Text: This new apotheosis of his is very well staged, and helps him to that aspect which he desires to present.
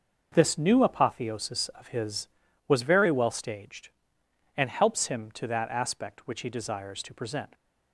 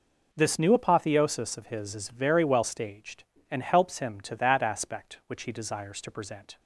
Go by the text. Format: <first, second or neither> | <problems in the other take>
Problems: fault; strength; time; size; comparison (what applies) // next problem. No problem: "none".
second | starts louder than the rest; until 1.3 s; 6 dB // says "was" for "is"; at 2.6 s